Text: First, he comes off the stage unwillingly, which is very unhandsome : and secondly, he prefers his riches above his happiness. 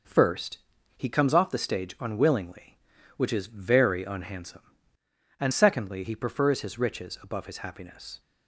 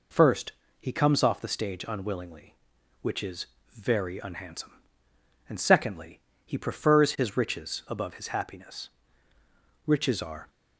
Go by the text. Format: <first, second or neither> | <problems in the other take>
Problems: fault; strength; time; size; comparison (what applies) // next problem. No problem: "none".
first | pauses between "is" and "very"; slight; at 3.4 s; 0.28 s long // goes on to say "Riches are"; noticeable; from 9.8 s on; 0.62 s long